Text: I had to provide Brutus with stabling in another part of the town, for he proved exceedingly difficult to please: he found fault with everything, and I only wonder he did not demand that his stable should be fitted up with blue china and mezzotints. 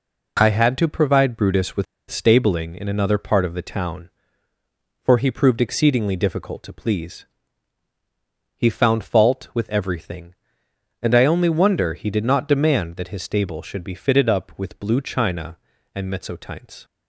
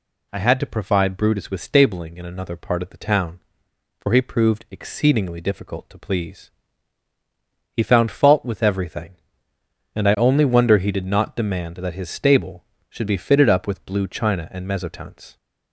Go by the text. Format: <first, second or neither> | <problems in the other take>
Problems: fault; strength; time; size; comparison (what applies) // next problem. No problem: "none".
second | pauses between "with" and "stabling"; slight; at 1.8 s; 0.25 s long